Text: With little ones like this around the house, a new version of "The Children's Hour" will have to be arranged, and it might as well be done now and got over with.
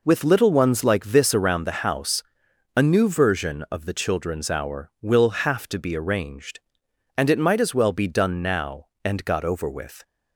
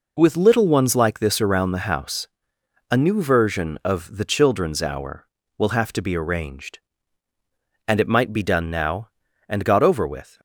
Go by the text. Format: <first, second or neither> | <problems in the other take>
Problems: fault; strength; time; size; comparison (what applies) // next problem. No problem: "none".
first | skips "as well"; at 8.3 s